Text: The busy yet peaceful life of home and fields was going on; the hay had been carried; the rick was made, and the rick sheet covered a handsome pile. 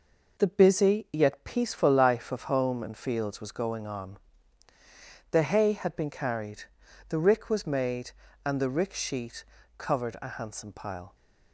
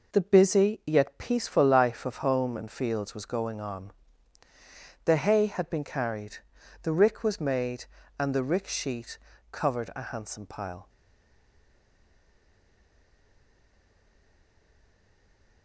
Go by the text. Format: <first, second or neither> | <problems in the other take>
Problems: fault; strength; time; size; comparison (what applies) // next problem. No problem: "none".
first | pauses between "sheet" and "covered"; slight; at 9.1 s; 0.32 s long; slight in the first // stays silent after the last word; strong; from 10.8 s on; 4.8 s long